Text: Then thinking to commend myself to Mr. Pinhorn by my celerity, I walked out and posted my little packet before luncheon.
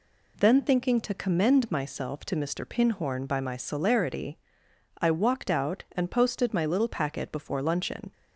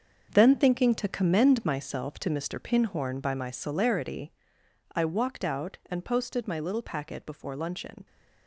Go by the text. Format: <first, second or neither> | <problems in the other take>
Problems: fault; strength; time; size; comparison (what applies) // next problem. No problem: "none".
first | gets quieter; strong; throughout; 10.5 dB